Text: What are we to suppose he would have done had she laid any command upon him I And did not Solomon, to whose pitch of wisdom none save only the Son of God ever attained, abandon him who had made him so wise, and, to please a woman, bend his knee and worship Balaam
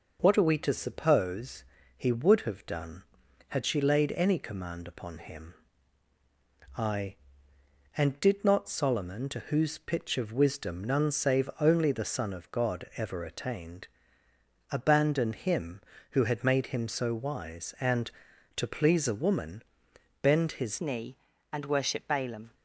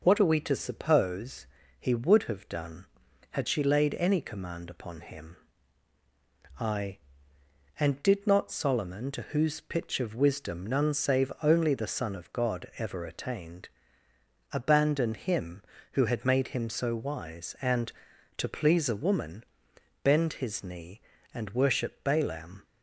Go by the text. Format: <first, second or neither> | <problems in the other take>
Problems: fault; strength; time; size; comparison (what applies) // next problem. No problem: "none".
second | pauses between "suppose" and "he"; slight; at 1.6 s; 0.32 s long; slight in the second // pauses between "him" and "I"; at 5.5 s; 1.2 s long; also in the second // changes voice at "knee"; from 20.7 s on; 1.8 s long